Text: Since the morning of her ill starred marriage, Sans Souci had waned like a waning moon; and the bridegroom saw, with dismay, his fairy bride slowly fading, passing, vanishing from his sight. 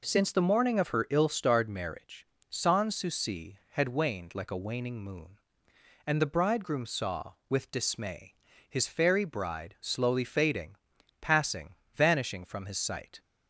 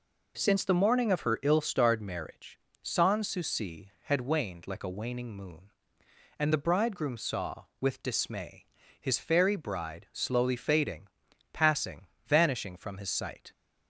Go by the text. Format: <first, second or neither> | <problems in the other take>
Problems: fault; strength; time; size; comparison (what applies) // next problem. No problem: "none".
neither | none